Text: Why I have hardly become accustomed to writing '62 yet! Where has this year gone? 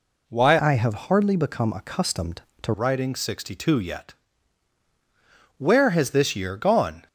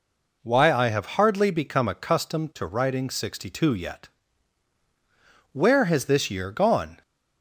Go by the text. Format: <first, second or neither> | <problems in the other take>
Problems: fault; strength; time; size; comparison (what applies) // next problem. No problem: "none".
second | changes voice from "I" to "to"; from 0.6 to 2.7 s; 2.1 s long